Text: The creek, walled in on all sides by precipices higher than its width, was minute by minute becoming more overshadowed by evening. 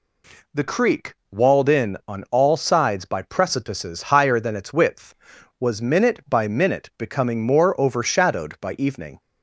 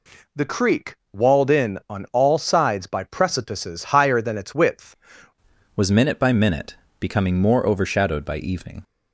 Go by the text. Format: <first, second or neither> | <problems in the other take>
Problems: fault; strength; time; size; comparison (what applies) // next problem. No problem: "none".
first | changes voice at "was"; from 5.7 s on; 3.1 s long // pauses between "minute" and "becoming"; slight; at 6.7 s; 0.24 s long